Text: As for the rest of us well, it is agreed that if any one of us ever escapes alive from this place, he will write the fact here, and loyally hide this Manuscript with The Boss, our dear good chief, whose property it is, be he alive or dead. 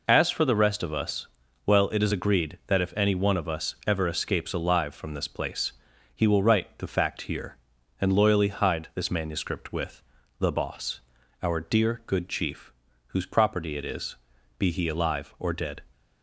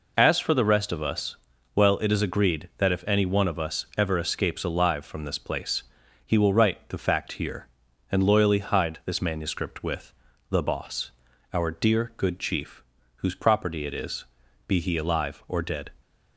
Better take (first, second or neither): neither